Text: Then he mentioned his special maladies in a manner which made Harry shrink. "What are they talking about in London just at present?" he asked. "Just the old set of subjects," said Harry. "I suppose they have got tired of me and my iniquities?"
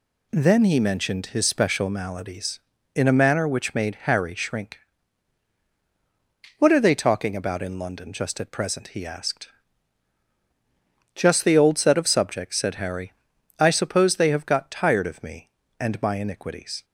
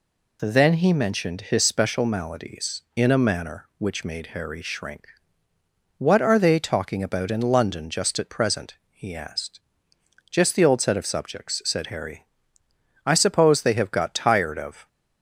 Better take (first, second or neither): first